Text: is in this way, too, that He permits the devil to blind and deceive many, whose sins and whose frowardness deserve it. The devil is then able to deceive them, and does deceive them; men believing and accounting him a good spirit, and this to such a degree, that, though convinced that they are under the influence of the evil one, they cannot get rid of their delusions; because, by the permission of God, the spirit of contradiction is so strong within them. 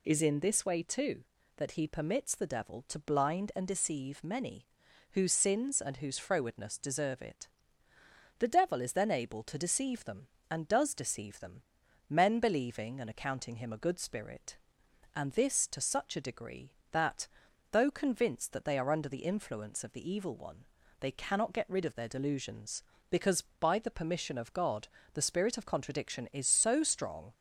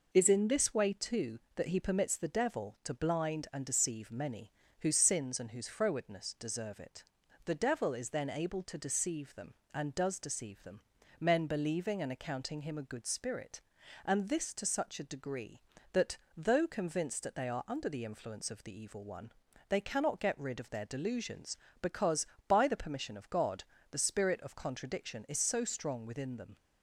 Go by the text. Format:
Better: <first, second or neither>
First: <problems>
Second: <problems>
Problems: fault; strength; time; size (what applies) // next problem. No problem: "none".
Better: second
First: stops before "within them"; at 27.3 s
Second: none